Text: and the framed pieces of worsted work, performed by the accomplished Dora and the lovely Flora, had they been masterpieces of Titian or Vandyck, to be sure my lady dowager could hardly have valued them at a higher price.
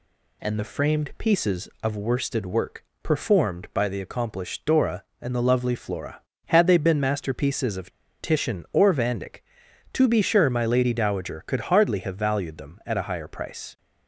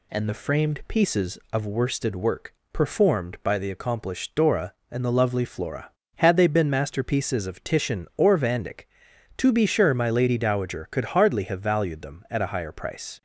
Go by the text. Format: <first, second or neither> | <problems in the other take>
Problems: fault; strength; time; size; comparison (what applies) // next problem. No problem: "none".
second | pauses between "of" and "Titian"; slight; at 7.9 s; 0.29 s long